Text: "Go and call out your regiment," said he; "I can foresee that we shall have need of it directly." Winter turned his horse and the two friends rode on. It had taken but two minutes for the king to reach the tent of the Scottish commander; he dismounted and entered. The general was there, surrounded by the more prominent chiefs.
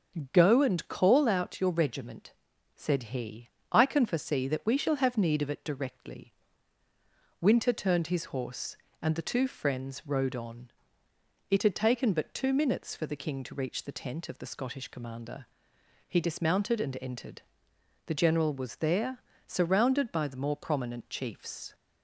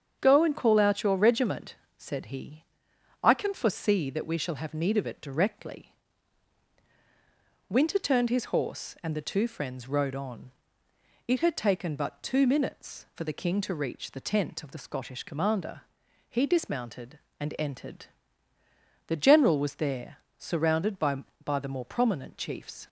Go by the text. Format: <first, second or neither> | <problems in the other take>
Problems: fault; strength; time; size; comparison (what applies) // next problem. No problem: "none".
first | starts louder than the rest; strong; until 1.2 s; 7.5 dB; strong in the first // says "by" twice; at 21.4 s